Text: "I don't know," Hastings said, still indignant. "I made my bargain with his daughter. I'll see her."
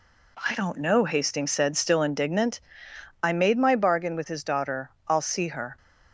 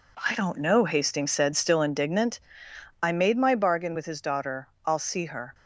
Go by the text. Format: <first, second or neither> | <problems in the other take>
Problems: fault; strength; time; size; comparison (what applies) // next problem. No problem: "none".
first | gets quieter; strong; throughout; 8 dB